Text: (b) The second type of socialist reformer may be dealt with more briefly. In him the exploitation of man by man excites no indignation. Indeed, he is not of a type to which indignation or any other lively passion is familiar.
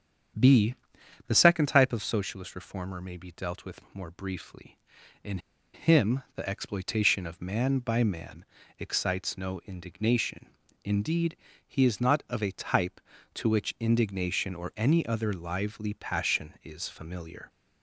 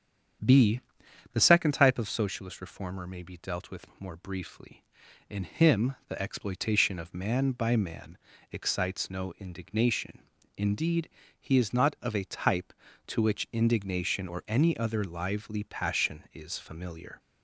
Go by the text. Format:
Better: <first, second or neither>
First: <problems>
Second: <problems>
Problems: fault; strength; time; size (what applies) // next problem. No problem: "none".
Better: second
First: starts louder than the rest; strong; until 1.9 s; 8 dB // pauses between "In" and "him"; slight; at 5.3 s; 0.35 s long // pauses between "man" and "excites"; slight; at 8.4 s; 0.34 s long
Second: starts louder than the rest; strong; until 1.9 s; 8 dB // pauses between "man" and "excites"; slight; at 8.1 s; 0.34 s long